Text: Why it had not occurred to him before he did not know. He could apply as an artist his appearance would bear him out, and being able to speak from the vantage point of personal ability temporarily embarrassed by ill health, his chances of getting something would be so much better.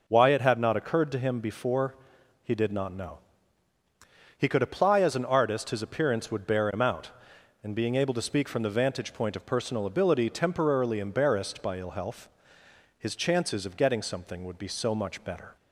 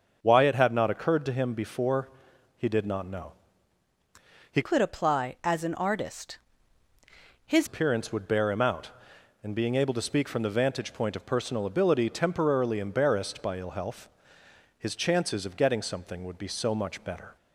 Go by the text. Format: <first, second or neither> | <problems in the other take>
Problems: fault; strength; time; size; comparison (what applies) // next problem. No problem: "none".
first | starts louder than the rest; until 1.2 s; 6.5 dB // pauses between "before" and "he"; noticeable; at 2.0 s; 0.48 s long; noticeable in the first // changes voice from "could" to "his"; from 4.6 to 7.6 s; 3.0 s long // pauses between "artist" and "his"; at 6.3 s; 1.0 s long